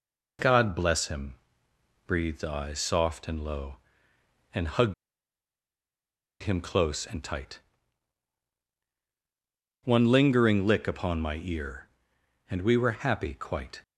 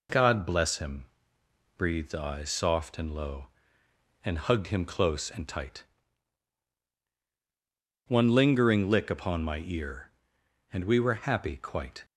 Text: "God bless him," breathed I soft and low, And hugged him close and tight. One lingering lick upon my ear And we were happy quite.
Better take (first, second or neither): second